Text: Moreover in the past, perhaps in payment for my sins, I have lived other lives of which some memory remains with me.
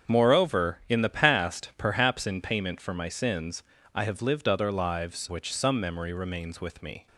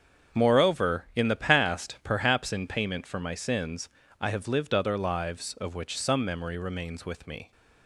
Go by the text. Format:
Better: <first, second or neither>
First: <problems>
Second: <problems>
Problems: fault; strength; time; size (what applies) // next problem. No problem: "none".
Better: second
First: starts louder than the rest; until 1.1 s; 7 dB // skips "of"; at 5.2 s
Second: starts louder than the rest; strong; until 1.4 s; 7 dB